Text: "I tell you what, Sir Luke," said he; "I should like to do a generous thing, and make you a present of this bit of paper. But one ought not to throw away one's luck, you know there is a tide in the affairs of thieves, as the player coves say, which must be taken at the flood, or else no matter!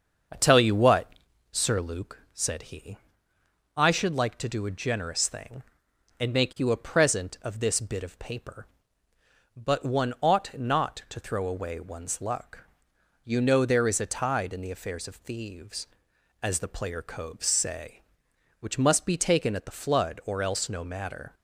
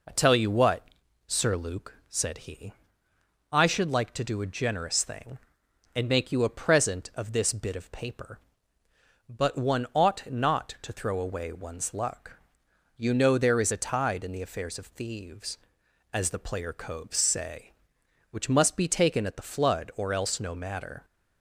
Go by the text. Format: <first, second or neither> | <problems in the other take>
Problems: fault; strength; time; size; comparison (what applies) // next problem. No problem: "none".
second | starts louder than the rest; until 1.7 s; 6.5 dB